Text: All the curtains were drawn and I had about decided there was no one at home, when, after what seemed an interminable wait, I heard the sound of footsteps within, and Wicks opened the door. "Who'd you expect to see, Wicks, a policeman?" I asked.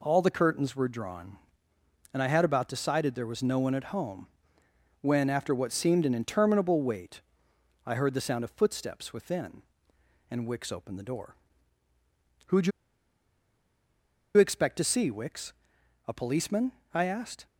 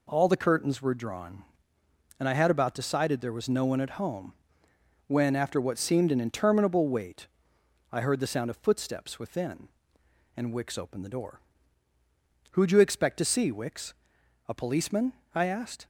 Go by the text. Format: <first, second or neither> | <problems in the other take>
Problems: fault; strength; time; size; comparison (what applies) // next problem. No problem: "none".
second | pauses between "you" and "expect"; strong; at 12.7 s; 1.6 s long